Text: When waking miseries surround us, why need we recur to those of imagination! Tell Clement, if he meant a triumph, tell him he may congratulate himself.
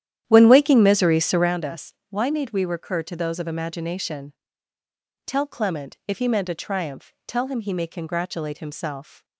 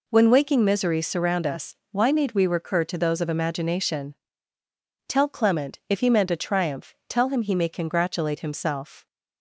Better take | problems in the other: second | starts louder than the rest; strong; until 1.6 s; 11 dB

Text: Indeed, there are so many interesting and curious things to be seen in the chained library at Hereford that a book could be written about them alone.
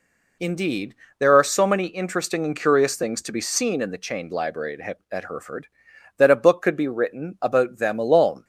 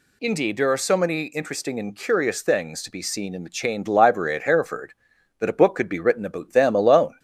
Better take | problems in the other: second | says "at" twice; at 5.1 s

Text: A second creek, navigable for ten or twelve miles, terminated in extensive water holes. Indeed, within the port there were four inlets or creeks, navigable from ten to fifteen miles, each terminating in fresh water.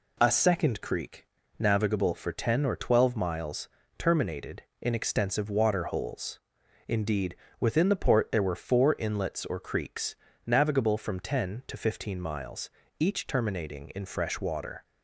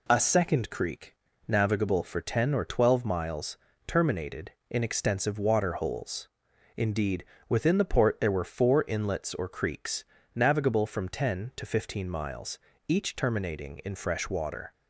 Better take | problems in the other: neither | none

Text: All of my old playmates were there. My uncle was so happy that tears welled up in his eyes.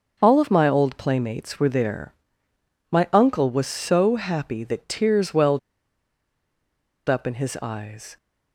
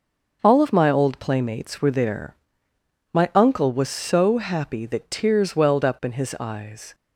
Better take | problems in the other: second | starts louder than the rest; until 1.2 s; 6 dB; noticeable in the second // pauses between "welled" and "up"; strong; at 5.5 s; 1.4 s long

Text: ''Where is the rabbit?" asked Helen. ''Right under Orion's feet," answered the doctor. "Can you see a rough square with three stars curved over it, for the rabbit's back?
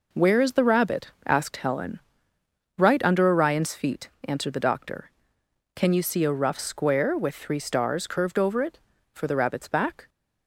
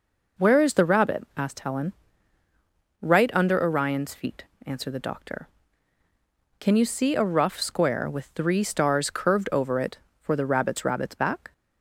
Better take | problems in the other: first | says "rabbit's" twice; at 10.8 s

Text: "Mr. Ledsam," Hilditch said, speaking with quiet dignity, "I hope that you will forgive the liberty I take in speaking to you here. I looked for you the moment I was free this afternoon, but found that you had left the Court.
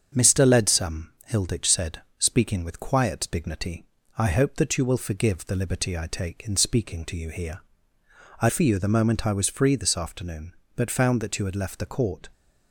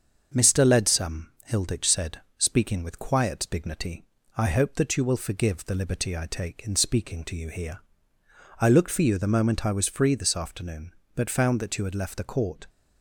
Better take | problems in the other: second | starts louder than the rest; strong; until 1.3 s; 7.5 dB; also in the second // skips "looked"; at 8.5 s

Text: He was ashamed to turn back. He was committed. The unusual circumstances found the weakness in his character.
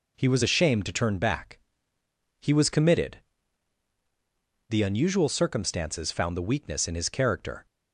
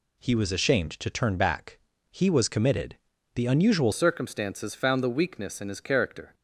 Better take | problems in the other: first | changes voice at "circumstances"; from 3.9 s on; 2.4 s long

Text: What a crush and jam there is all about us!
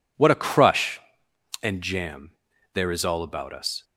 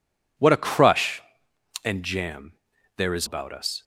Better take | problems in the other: first | pauses between "jam" and "there"; at 2.5 s; 0.44 s long; also in the first // skips "all"; at 3.2 s

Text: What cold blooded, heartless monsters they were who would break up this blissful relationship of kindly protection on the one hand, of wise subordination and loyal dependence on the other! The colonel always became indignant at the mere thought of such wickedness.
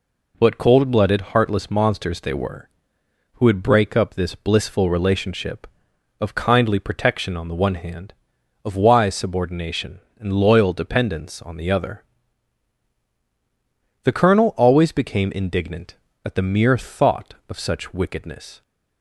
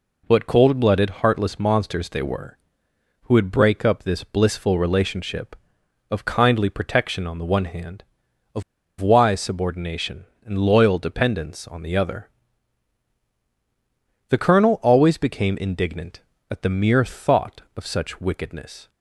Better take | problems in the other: first | pauses between "of" and "wise"; at 8.6 s; 0.38 s long

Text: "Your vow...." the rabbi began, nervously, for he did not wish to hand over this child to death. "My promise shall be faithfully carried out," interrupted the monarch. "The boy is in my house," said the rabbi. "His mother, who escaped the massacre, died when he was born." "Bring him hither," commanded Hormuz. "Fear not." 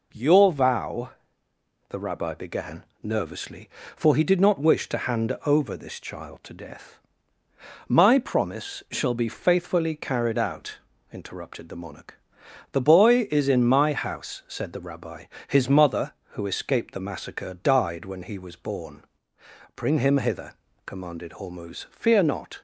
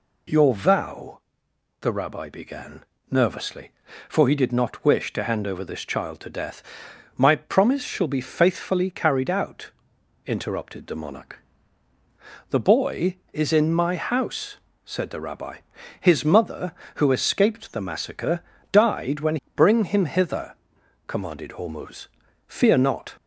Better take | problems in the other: first | skips "he was born"; at 19.4 s

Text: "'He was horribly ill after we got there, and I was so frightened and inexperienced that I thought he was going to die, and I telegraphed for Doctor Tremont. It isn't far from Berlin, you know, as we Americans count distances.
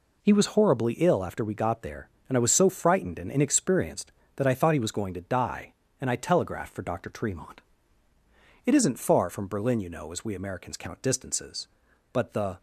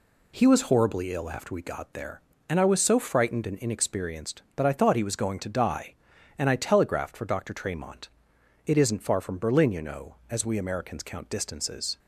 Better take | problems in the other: second | goes on to say "But the"; slight; from 12.1 s on; 0.48 s long

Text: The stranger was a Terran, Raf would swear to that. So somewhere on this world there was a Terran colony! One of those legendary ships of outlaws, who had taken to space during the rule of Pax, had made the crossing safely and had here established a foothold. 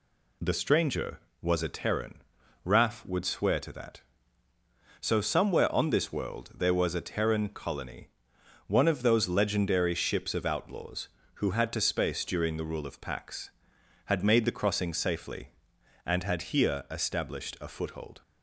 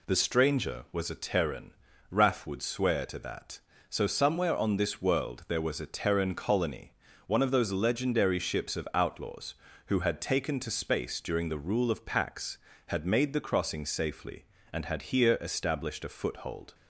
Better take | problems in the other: second | skips "taken"; at 11.7 s

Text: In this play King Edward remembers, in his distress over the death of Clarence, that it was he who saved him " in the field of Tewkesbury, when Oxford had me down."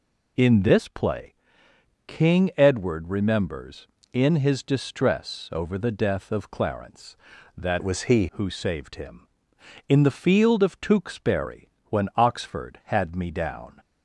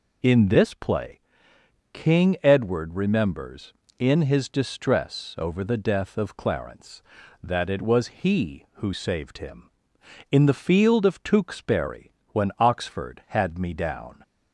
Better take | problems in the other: second | pauses between "play" and "King"; noticeable; at 1.3 s; 0.72 s long; noticeable in the second // changes voice from "it" to "he"; from 7.7 to 8.2 s; 0.5 s long

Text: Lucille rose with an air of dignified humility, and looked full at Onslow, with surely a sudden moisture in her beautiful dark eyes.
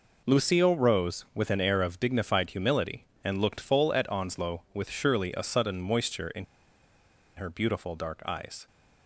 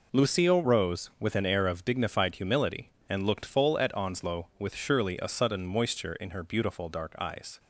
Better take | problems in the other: second | pauses between "in" and "her"; noticeable; at 6.4 s; 0.91 s long

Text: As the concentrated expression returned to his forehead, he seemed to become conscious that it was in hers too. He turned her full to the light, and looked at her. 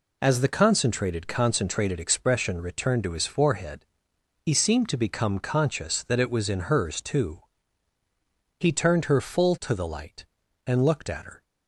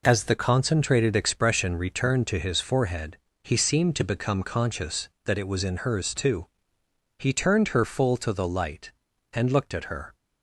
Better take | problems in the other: second | says "concentrated" twice; at 1.2 s

